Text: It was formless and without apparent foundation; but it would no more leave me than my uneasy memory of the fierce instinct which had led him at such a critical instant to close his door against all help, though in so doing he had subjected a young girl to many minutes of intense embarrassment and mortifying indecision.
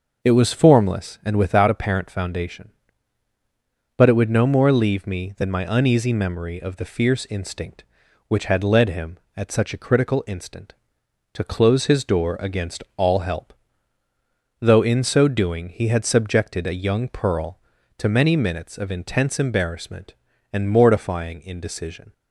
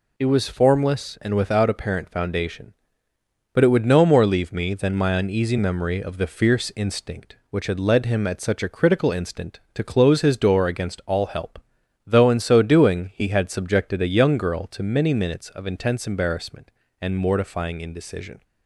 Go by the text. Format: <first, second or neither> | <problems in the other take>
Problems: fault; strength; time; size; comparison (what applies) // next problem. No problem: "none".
second | starts louder than the rest; noticeable; until 1.3 s; 6 dB // says "pearl" for "girl"; at 17.0 s